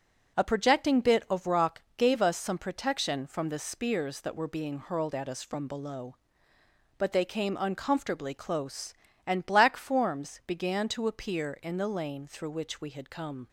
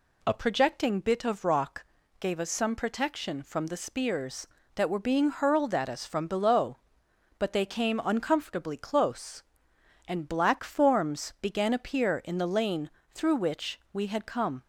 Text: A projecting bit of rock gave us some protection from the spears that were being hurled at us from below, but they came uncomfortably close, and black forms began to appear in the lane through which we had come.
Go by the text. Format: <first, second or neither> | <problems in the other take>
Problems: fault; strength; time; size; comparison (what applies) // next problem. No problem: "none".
first | pauses between "rock" and "gave"; slight; at 1.8 s; 0.34 s long; slight in the first // skips "to"; at 11.7 s // pauses between "lane" and "through"; slight; at 12.8 s; 0.22 s long